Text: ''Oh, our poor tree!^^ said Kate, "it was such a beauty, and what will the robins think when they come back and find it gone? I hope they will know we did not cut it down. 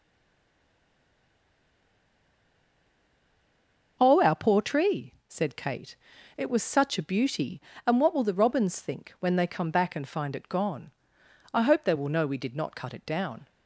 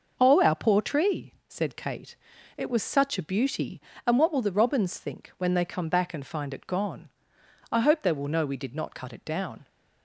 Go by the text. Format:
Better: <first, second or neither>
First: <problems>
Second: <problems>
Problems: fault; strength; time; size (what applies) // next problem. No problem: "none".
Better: second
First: stays silent before the first word; strong; until 3.9 s; 3.9 s long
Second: none